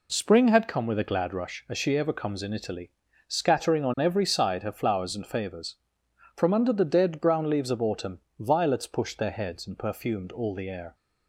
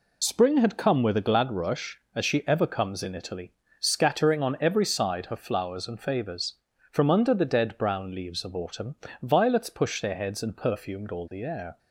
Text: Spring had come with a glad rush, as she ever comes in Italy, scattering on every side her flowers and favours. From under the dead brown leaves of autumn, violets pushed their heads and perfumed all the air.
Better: first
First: none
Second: loses the start of "Spring"; at 0.2 s; 25 ms

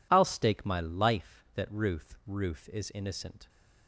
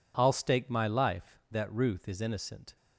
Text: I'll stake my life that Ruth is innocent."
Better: second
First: says "Ruth" twice; at 2.2 s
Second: none

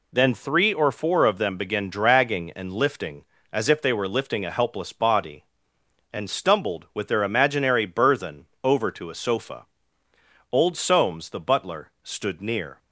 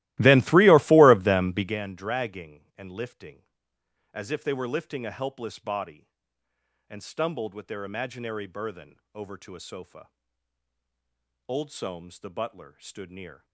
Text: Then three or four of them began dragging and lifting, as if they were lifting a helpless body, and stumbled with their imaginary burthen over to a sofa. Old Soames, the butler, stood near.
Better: first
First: pauses between "burthen" and "over"; slight; at 8.4 s; 0.18 s long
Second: starts louder than the rest; strong; until 1.8 s; 17 dB // pauses between "burthen" and "over"; slight; at 8.9 s; 0.18 s long

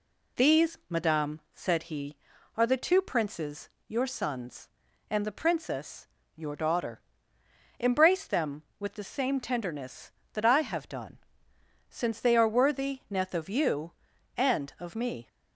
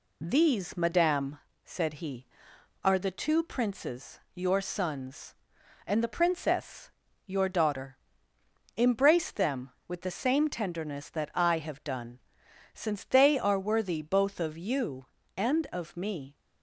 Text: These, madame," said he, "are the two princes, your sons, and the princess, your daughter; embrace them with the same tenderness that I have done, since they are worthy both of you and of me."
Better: second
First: says "neth" for "both"; at 13.1 s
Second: none

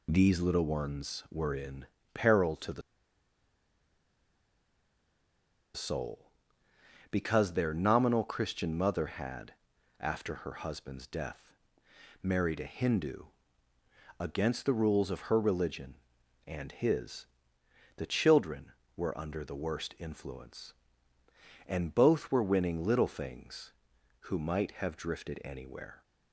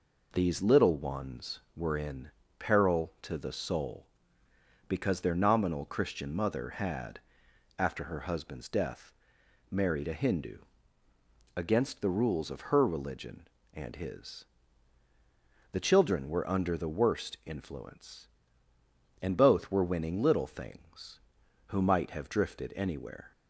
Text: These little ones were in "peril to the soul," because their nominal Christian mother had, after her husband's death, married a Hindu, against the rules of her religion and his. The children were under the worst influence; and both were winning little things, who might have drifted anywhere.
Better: second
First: pauses between "in" and "peril"; slight; at 1.8 s; 0.28 s long // pauses between "the" and "soul"; strong; at 2.8 s; 2.9 s long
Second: pauses between "in" and "peril"; slight; at 2.3 s; 0.26 s long

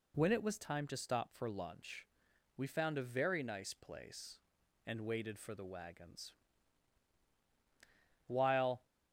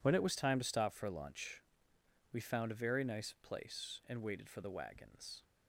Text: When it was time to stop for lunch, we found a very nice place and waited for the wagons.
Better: second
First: goes on to say "While"; from 8.2 s on; 0.60 s long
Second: none

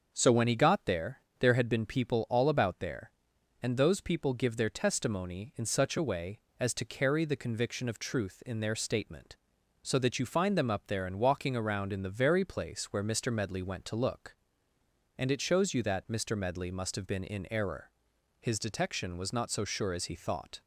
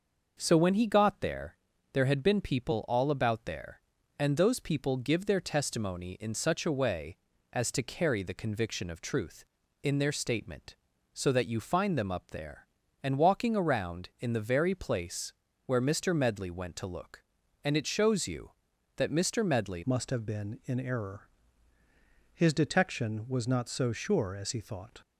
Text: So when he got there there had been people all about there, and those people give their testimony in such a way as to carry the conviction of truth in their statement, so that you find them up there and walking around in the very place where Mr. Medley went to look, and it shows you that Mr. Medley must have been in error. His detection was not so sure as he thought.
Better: first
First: starts louder than the rest; until 1.1 s; 6.5 dB // pauses between "there" and "there"; slight; at 1.2 s; 0.18 s long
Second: starts louder than the rest; noticeable; until 1.4 s; 6 dB // pauses between "there" and "there"; at 1.5 s; 0.38 s long // pauses between "place" and "where"; slight; at 15.3 s; 0.34 s long // changes voice at "must"; from 19.8 s on; 5.2 s long

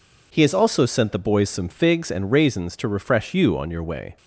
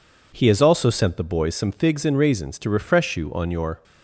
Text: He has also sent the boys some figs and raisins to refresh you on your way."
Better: first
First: none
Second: stops before "way"; at 3.8 s

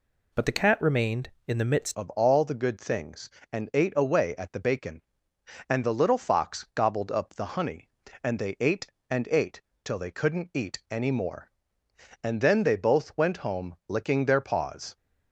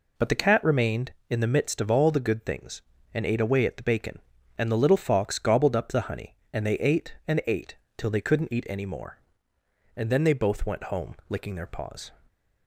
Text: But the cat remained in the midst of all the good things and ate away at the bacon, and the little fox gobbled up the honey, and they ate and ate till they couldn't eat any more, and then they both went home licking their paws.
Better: second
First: changes voice at "of"; from 1.9 s on; 13.0 s long // pauses between "ate" and "till"; slight; at 9.6 s; 0.24 s long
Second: pauses between "ate" and "till"; slight; at 7.7 s; 0.20 s long

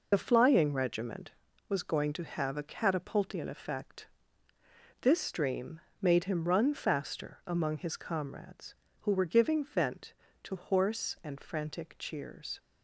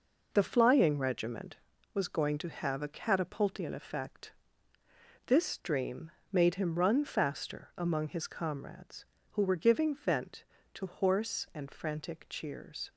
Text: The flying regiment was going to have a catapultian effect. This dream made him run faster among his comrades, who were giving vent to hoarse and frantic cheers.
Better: second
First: loses the start of "The"; at 0.1 s; 45 ms // pauses between "dream" and "made"; slight; at 5.7 s; 0.22 s long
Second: pauses between "dream" and "made"; slight; at 6.0 s; 0.22 s long

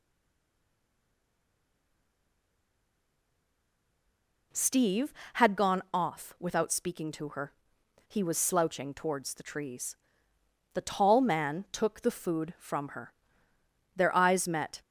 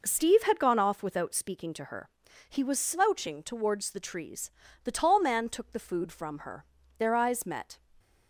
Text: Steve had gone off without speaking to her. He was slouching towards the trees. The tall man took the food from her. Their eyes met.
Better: second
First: stays silent before the first word; strong; until 4.5 s; 4.5 s long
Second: none

